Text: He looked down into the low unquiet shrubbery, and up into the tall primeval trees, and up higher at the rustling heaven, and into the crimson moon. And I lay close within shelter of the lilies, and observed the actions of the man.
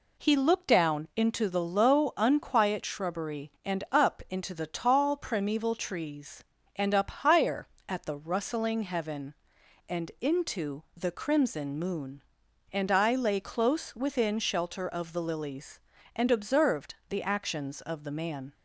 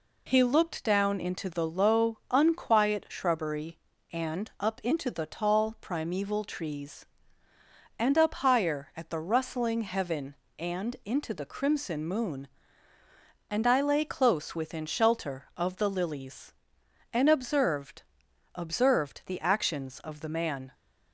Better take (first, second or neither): first